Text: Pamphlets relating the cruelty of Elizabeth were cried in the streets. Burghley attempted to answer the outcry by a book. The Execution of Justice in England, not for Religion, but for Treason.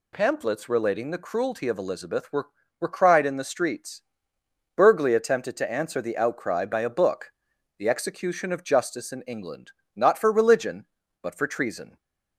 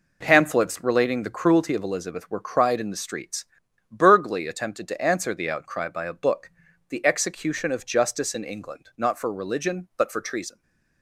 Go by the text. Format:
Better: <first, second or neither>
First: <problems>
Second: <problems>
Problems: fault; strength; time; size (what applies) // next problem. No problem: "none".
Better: second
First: says "were" twice; at 2.8 s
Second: none